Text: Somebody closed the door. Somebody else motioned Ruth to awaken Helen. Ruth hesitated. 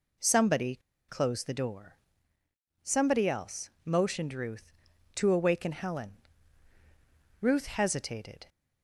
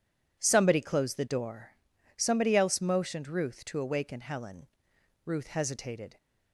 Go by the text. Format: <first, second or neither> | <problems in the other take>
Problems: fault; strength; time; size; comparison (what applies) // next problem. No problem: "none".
second | pauses between "Somebody" and "closed"; slight; at 0.7 s; 0.28 s long